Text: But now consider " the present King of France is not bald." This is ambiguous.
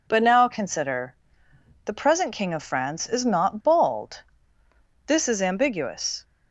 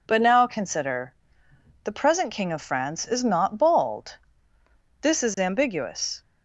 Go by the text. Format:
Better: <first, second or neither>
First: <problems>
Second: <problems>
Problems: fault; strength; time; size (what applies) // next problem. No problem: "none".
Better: neither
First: none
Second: none